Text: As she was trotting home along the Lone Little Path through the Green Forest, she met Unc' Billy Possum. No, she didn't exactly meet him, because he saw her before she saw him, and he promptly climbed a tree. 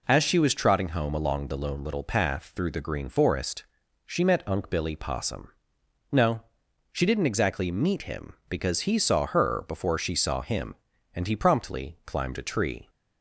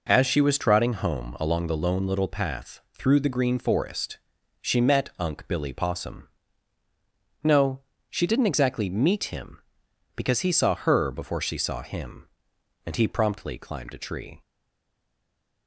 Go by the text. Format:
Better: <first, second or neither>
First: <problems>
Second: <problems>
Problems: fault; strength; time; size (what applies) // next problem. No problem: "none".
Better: first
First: none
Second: pauses between "Path" and "through"; slight; at 2.7 s; 0.18 s long // stays silent after the last word; noticeable; from 14.4 s on; 1.2 s long